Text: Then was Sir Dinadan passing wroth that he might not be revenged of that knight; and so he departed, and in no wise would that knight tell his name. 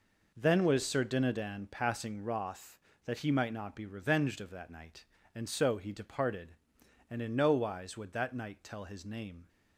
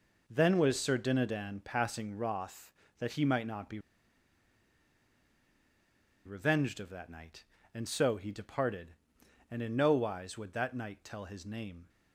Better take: first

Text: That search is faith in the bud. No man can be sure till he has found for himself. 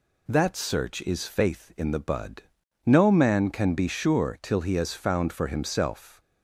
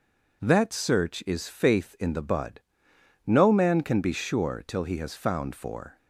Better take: first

